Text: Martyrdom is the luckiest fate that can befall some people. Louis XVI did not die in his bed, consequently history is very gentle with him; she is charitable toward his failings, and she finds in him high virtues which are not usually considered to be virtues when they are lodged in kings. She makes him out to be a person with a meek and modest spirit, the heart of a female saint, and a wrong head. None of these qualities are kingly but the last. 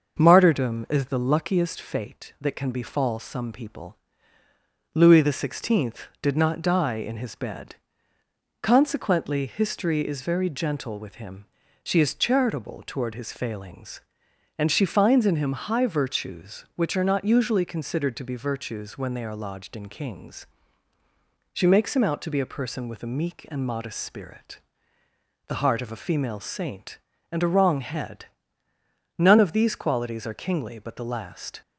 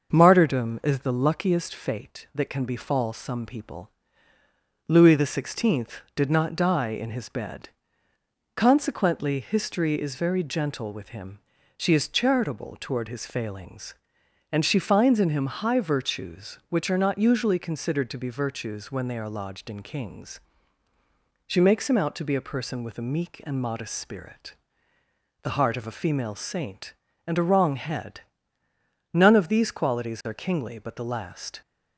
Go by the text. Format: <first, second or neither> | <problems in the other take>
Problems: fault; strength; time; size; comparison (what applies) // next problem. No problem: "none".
neither | starts louder than the rest; the same in both